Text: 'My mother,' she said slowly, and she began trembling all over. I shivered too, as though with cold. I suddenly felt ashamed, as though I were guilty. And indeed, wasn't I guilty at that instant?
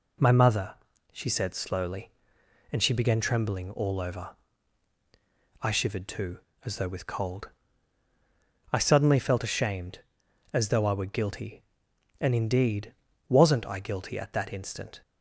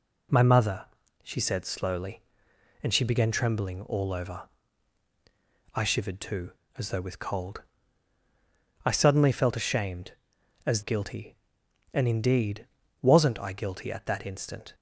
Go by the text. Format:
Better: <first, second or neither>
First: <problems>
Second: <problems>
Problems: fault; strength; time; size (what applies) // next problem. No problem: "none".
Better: first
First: none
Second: skips "though I were"; at 10.8 s